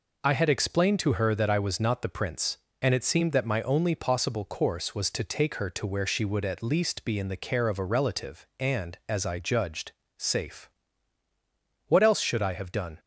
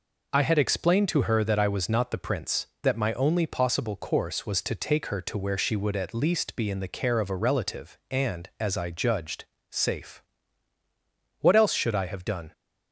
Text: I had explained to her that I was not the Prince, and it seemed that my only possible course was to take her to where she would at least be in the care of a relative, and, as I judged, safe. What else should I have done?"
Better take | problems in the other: first | skips "and it seemed"; at 2.7 s

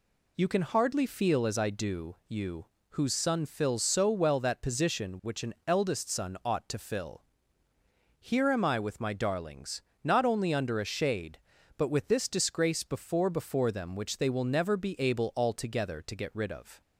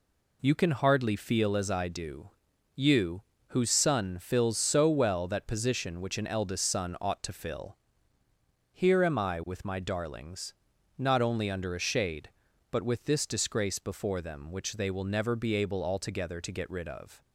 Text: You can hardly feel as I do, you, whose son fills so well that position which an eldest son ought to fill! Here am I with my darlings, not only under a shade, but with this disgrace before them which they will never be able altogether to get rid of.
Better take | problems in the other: second | says "before" twice; at 13.2 s

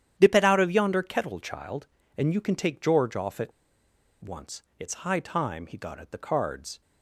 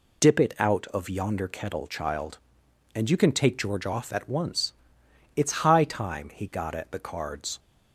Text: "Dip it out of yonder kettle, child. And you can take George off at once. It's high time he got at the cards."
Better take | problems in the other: second | starts louder than the rest; strong; until 1.1 s; 10 dB // pauses between "at" and "once"; noticeable; at 3.5 s; 0.71 s long

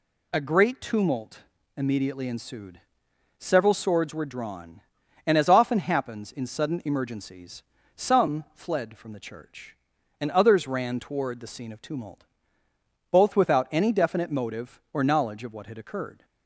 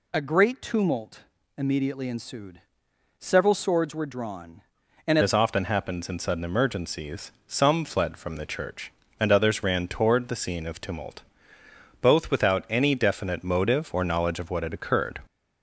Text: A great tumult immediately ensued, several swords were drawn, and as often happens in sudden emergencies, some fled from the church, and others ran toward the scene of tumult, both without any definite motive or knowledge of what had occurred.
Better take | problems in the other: first | pauses between "tumult" and "immediately"; slight; at 1.1 s; 0.36 s long; slight in the first // changes voice at "as"; from 5.2 s on; 9.9 s long

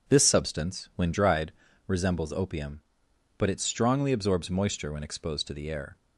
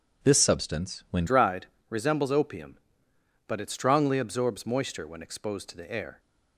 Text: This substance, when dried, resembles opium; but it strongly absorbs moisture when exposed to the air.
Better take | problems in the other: first | changes voice at "dried"; from 1.2 s on; 4.9 s long

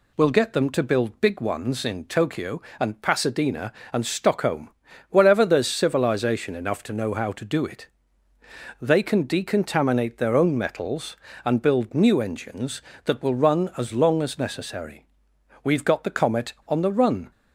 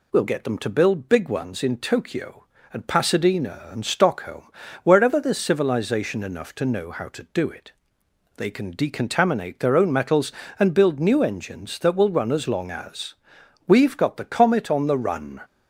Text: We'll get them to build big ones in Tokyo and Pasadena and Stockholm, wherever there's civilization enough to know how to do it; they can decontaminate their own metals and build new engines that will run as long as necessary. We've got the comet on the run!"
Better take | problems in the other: first | skips "necessary"; at 13.4 s

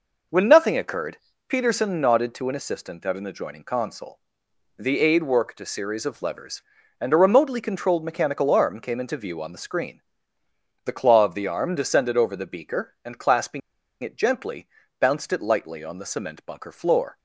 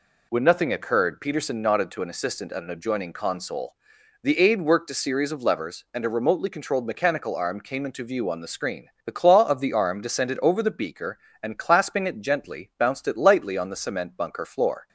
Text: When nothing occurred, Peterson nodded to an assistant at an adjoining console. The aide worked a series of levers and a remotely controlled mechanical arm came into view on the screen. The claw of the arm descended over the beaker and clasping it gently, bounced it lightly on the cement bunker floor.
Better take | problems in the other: second | pauses between "clasping" and "it"; at 13.6 s; 0.43 s long

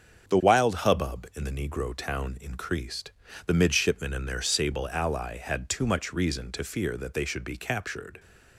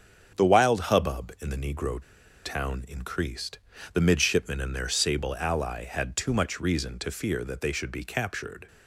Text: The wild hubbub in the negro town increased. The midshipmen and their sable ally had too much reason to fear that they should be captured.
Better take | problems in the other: first | starts louder than the rest; strong; until 1.5 s; 8 dB; strong in the first // pauses between "negro" and "town"; at 2.0 s; 0.43 s long

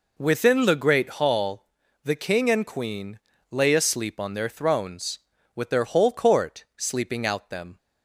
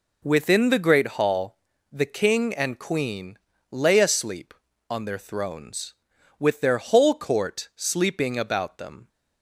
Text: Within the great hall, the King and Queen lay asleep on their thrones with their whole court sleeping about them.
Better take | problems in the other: second | pauses between "Queen" and "lay"; slight; at 3.1 s; 0.32 s long; slight in the second // says "out" for "about"; at 7.2 s

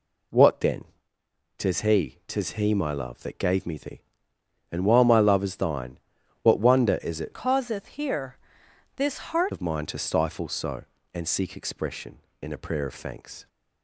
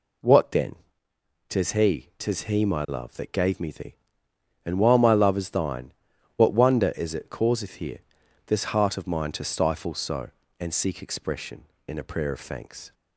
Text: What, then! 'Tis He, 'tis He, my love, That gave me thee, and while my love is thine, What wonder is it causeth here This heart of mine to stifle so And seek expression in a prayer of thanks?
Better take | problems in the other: second | changes voice from "causeth" to "heart"; from 7.3 to 9.5 s; 2.2 s long // pauses between "here" and "This"; noticeable; at 8.3 s; 0.58 s long; noticeable in the second

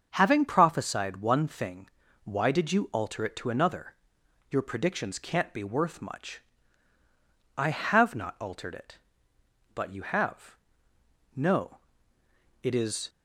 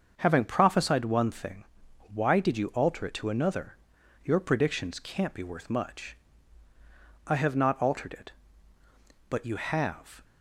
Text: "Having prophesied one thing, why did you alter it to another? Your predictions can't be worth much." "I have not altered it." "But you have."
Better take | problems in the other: second | starts louder than the rest; until 1.1 s; 6.5 dB; also in the second // goes on to say "No It is"; strong; from 11.3 s on; 1.7 s long

